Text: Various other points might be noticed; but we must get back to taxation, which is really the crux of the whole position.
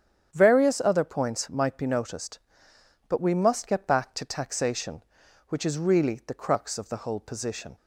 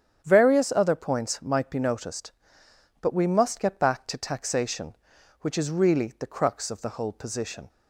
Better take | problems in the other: neither | starts louder than the rest; strong; the same in both

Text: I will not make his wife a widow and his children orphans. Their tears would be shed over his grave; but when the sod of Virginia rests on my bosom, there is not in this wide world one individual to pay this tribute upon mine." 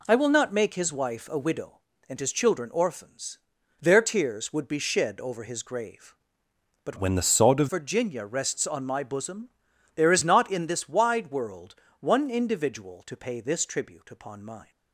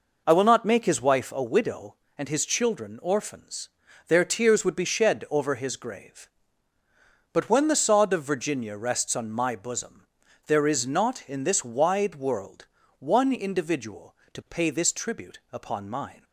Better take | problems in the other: second | changes voice from "when" to "of"; from 6.9 to 7.6 s; 0.7 s long // pauses between "world" and "one"; slight; at 11.7 s; 0.26 s long; slight in the second

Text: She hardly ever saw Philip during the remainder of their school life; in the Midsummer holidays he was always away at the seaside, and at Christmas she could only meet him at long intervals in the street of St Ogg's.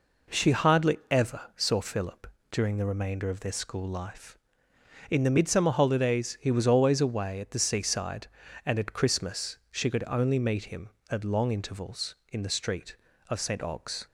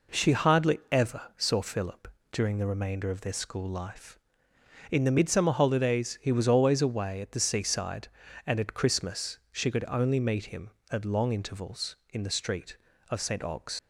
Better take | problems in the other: first | pauses between "ever" and "saw"; slight; at 1.2 s; 0.16 s long; slight in the first // pauses between "Philip" and "during"; slight; at 2.0 s; 0.24 s long; slight in the first // leaves "Ogg's" unfinished; at 13.7 s; 75 ms

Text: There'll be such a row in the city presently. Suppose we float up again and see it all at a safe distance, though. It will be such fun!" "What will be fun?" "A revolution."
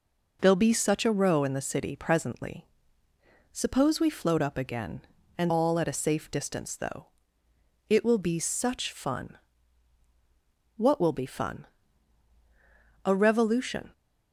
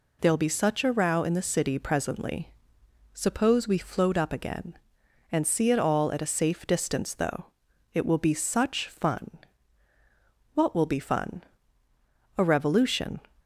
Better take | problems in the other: second | skips "see it"; at 5.5 s

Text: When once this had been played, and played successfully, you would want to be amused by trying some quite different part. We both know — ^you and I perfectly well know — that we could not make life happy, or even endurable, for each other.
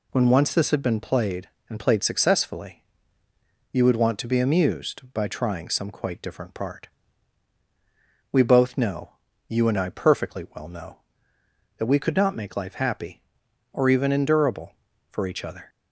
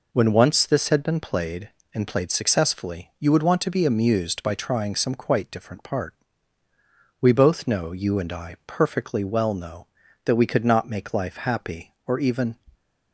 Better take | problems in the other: first | stops before "endurable for each other"; at 12.7 s

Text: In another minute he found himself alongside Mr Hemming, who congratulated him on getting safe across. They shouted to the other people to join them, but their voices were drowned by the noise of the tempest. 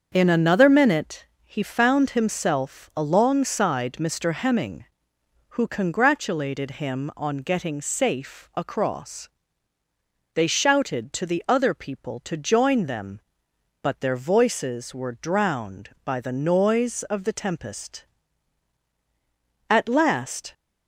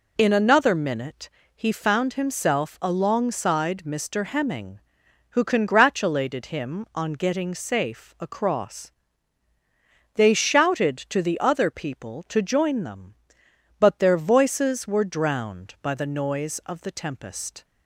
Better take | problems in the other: second | starts louder than the rest; until 1.1 s; 7 dB // pauses between "minute" and "he"; slight; at 1.2 s; 0.18 s long; slight in the second // goes on to say "At last"; noticeable; from 19.7 s on; 0.82 s long

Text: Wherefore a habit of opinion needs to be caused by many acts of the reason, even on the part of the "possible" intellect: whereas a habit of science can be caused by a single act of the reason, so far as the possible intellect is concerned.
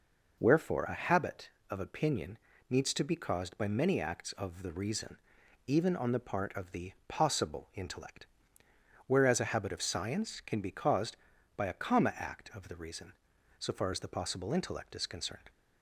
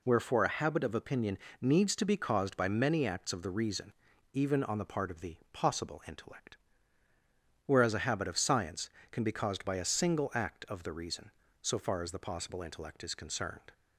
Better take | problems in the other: second | pauses between "opinion" and "needs"; slight; at 2.3 s; 0.32 s long; slight in the second // pauses between "the" and "possible"; slight; at 6.9 s; 0.16 s long; slight in the second // says "comma" for "single"; at 11.7 s

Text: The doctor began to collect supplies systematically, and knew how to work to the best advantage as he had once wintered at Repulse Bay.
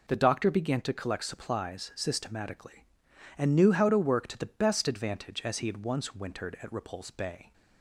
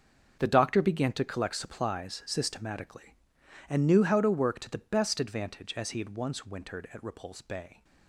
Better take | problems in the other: first | gets quieter; strong; throughout; 13 dB

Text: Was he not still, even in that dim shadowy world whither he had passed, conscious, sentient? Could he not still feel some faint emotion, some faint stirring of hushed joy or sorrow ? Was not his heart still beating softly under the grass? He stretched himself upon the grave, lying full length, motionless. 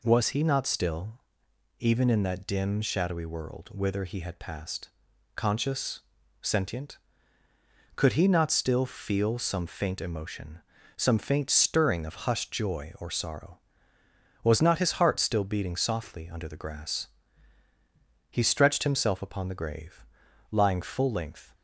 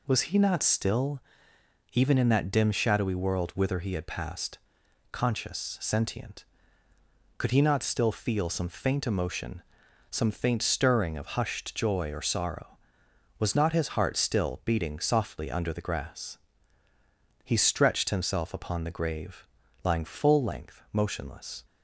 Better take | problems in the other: second | stops before "motionless"; at 21.5 s

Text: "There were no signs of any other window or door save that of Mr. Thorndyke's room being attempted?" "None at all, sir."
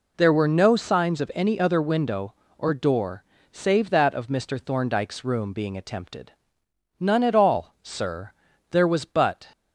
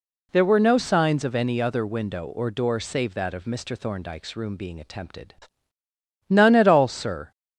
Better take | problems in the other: second | pauses between "door" and "save"; slight; at 3.2 s; 0.28 s long // goes on to say "There was but"; noticeable; from 8.6 s on; 0.78 s long

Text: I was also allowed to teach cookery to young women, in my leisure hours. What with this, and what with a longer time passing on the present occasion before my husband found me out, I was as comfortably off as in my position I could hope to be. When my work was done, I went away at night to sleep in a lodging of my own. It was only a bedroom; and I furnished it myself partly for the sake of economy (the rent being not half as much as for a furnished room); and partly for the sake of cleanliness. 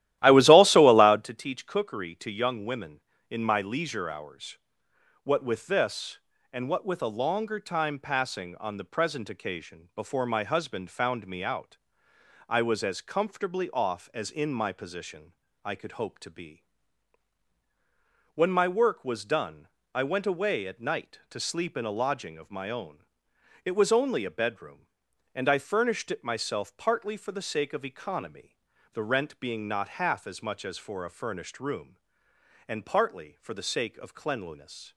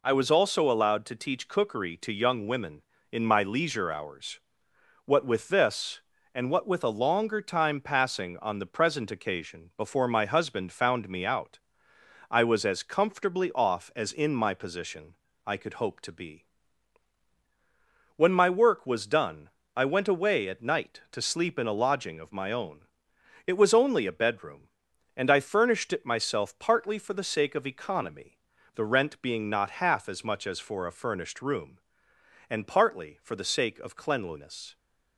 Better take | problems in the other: second | starts louder than the rest; strong; until 1.4 s; 14 dB // pauses between "position" and "I"; slight; at 15.3 s; 0.30 s long; slight in the second

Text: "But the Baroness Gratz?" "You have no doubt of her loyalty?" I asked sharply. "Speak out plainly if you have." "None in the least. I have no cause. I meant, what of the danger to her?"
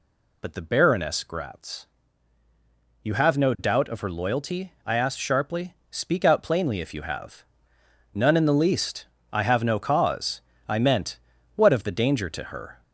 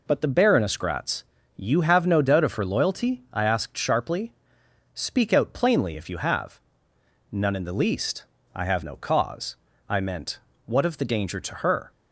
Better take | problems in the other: second | gets louder; slight; throughout; 3 dB

